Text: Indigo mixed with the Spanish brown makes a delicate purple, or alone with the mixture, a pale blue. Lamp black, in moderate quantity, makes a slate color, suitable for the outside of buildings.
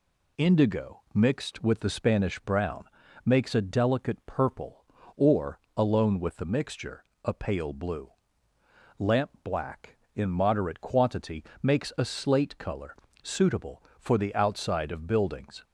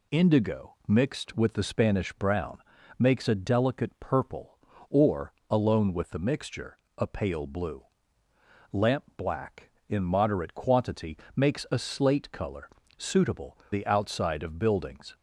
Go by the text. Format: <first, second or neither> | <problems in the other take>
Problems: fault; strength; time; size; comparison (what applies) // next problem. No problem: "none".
first | pauses between "brown" and "makes"; at 2.5 s; 0.40 s long; also in the first // pauses between "or" and "alone"; slight; at 5.3 s; 0.16 s long; slight in the first // skips "for"; at 13.6 s